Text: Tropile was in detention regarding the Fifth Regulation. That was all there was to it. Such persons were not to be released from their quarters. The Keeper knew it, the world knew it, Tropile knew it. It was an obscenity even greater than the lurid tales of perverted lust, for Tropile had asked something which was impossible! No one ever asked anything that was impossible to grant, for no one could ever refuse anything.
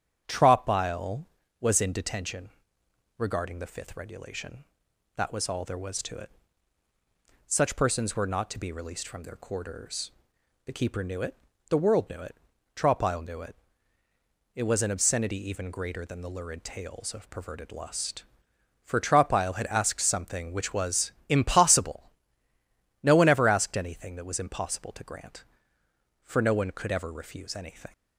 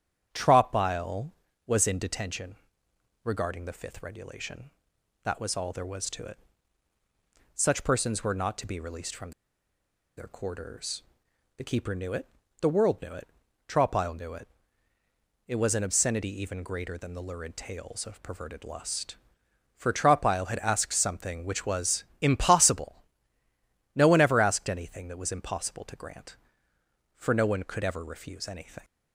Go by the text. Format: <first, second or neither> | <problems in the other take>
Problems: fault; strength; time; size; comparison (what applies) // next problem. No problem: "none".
first | starts louder than the rest; strong; until 1.6 s; 8.5 dB; strong in the first // pauses between "detention" and "regarding"; noticeable; at 2.5 s; 0.70 s long; noticeable in the first // pauses between "from" and "their"; noticeable; at 9.3 s; 0.86 s long // pauses between "was" and "impossible"; slight; at 22.0 s; 0.16 s long; slight in the first